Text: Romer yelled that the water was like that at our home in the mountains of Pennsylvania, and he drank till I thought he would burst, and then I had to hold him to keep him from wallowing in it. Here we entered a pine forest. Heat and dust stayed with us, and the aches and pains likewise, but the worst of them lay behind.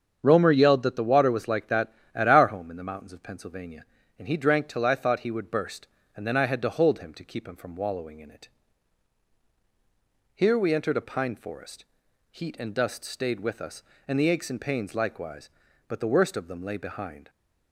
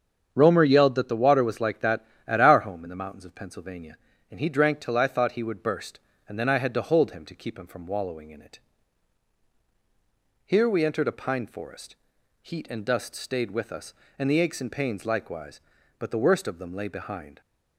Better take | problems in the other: neither | starts louder than the rest; strong; the same in both

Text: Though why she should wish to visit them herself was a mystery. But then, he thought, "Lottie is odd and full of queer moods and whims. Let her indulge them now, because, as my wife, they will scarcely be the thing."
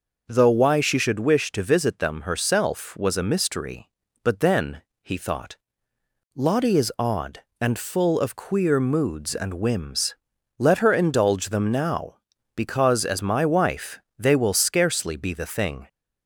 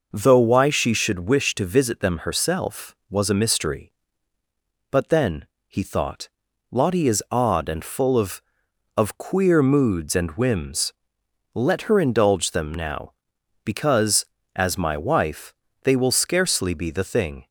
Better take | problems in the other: first | says "of" twice; at 8.9 s

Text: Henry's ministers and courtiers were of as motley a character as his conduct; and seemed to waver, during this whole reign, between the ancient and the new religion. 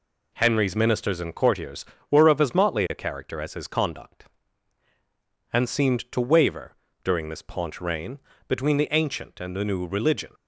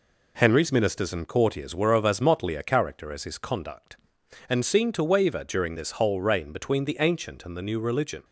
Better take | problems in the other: second | says "paunch" for "whole"; at 7.4 s

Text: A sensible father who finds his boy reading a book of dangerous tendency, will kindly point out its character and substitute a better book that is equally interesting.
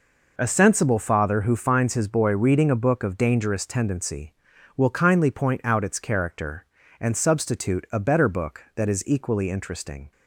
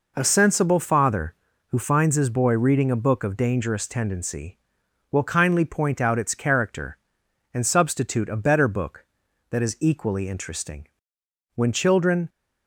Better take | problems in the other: first | goes on to say "When children"; noticeable; from 11.5 s on; 0.72 s long

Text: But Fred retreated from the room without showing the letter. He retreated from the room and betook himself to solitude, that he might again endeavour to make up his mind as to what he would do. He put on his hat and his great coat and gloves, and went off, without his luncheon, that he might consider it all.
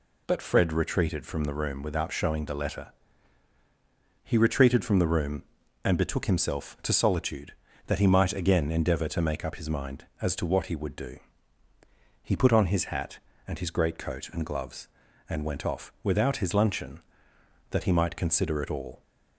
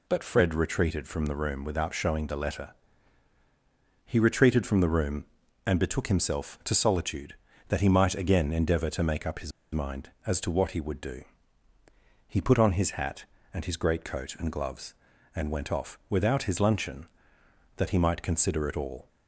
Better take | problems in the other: first | pauses between "his" and "mind"; slight; at 9.5 s; 0.22 s long

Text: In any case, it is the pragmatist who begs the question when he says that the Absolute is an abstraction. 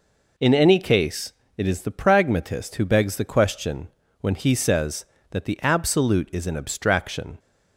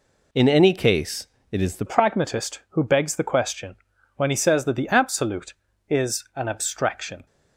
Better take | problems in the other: first | changes voice at "pragmatist"; from 1.8 s on; 5.4 s long // pauses between "question" and "when"; at 3.7 s; 0.40 s long; slight in the first

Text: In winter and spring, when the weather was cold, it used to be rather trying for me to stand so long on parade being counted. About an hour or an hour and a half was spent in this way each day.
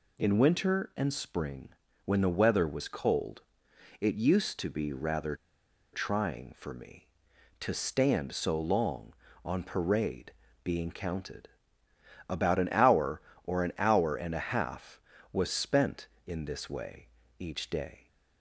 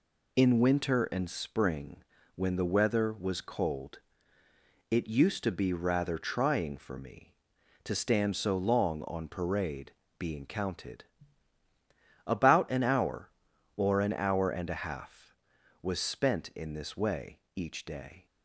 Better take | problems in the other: second | pauses between "rather" and "trying"; noticeable; at 5.3 s; 0.57 s long // pauses between "parade" and "being"; slight; at 10.3 s; 0.32 s long; slight in the second // pauses between "way" and "each"; slight; at 17.0 s; 0.30 s long; slight in the second

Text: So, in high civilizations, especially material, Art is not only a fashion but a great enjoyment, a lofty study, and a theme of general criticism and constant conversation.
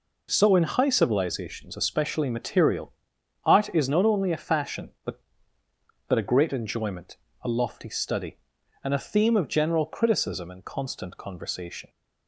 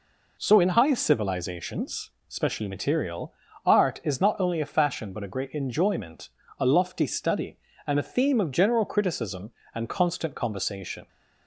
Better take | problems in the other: second | says "but" twice; at 6.0 s

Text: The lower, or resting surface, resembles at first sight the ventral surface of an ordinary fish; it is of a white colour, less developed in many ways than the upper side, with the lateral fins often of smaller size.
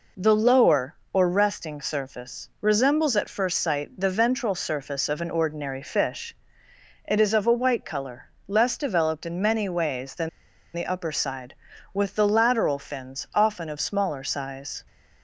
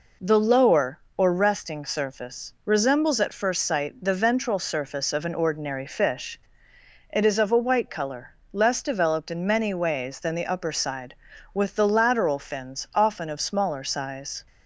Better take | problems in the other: second | pauses between "than" and "the"; at 10.2 s; 0.45 s long

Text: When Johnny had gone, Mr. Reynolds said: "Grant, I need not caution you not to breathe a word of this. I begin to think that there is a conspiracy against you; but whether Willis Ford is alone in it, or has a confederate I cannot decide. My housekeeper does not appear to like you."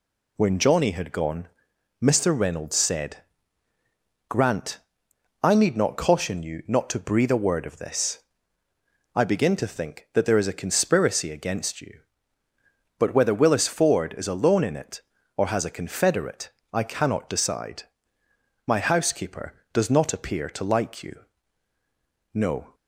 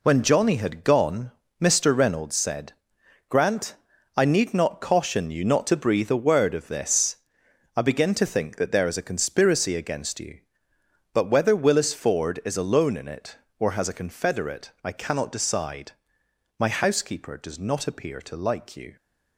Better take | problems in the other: second | pauses between "confederate" and "I"; slight; at 16.5 s; 0.20 s long // goes on to say "No"; slight; from 22.3 s on; 0.40 s long

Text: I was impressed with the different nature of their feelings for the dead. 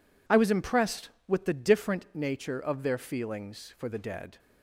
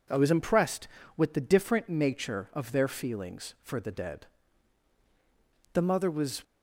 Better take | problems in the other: first | goes on to say "The mother was"; noticeable; from 5.7 s on; 0.70 s long

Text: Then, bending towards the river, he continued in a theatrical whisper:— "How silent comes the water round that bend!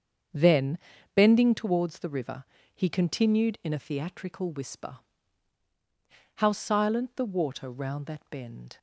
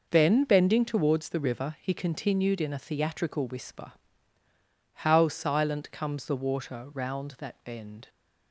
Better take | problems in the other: second | starts louder than the rest; strong; until 1.6 s; 7.5 dB // skips "comes"; at 7.1 s

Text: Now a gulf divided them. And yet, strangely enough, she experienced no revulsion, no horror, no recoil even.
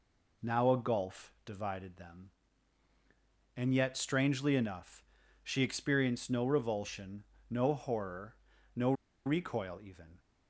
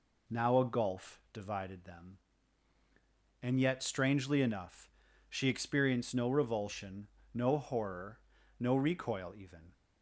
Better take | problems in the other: second | pauses between "no" and "recoil"; slight; at 8.9 s; 0.32 s long

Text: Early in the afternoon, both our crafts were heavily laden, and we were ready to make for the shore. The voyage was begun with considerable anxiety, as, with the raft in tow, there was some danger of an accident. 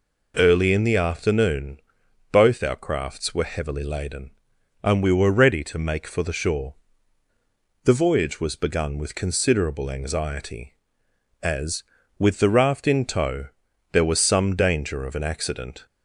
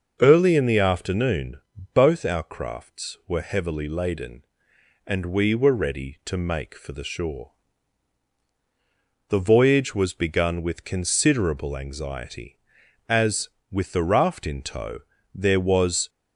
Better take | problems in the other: first | starts louder than the rest; until 1.2 s; 6 dB // stops before "some danger of an accident"; at 16.0 s

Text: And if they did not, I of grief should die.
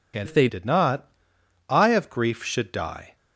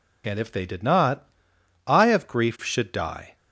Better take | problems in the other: second | changes voice from "if" to "they"; from 0.2 to 0.4 s; 0.2 s long

